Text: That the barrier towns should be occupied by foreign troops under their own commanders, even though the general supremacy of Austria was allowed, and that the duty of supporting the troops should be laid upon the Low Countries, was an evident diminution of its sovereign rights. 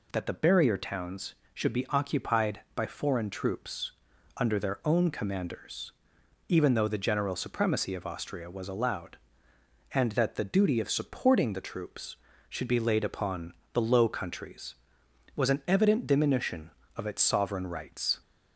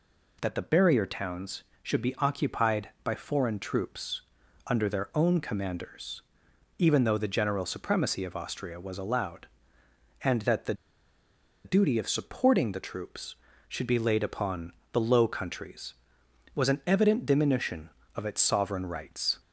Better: first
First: pauses between "troops" and "under"; noticeable; at 3.9 s; 0.46 s long // pauses between "upon" and "the"; slight; at 13.5 s; 0.20 s long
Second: pauses between "troops" and "under"; noticeable; at 4.2 s; 0.46 s long // pauses between "the" and "duty"; noticeable; at 10.7 s; 0.91 s long // pauses between "upon" and "the"; slight; at 14.7 s; 0.20 s long

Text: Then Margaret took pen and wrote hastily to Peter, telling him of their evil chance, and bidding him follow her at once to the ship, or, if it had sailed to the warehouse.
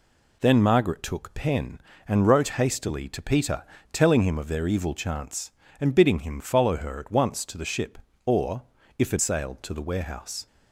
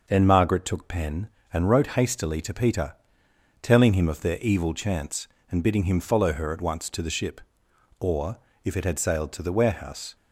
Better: second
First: skips "had"; at 9.1 s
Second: none

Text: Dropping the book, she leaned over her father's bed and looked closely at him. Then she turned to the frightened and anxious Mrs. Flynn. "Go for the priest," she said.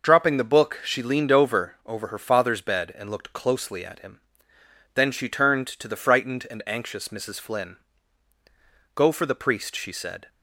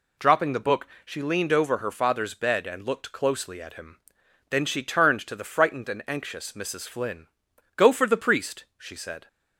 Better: second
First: says "over" twice; at 1.8 s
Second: none

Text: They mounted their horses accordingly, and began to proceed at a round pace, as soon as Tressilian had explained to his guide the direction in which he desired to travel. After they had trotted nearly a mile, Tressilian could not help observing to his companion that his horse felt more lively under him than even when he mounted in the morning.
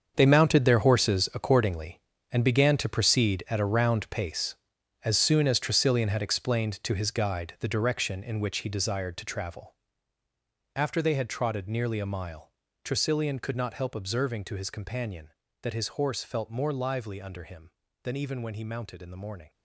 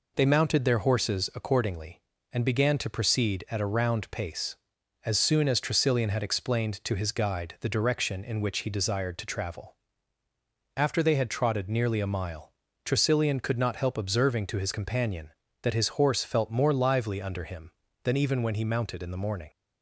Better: second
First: gets quieter; strong; throughout; 12.5 dB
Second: none

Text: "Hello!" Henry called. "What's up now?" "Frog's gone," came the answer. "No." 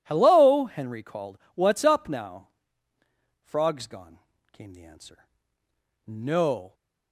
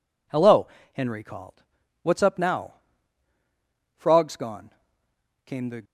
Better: first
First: none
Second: stops before "answer No"; at 5.8 s

